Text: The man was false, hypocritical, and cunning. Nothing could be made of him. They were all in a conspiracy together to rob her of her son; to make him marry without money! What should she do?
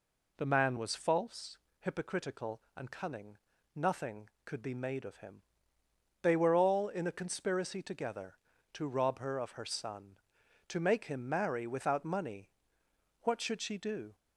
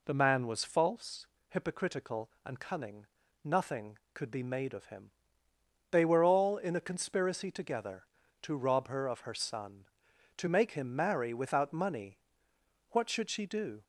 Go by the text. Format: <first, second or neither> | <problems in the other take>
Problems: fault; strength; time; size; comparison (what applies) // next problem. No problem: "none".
neither | none